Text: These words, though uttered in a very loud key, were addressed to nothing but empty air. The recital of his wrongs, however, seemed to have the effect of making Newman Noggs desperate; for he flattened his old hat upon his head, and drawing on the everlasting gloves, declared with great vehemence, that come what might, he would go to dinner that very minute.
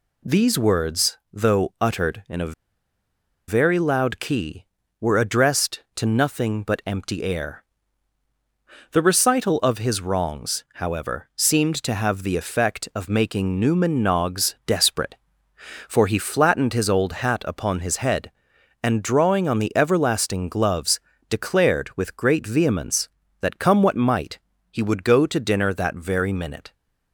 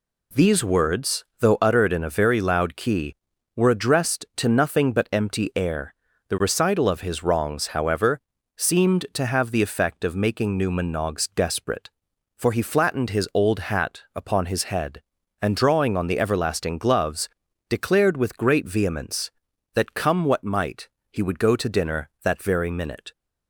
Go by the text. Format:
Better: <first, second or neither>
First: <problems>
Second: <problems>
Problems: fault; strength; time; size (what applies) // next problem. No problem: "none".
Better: second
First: pauses between "a" and "very"; noticeable; at 2.5 s; 0.94 s long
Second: none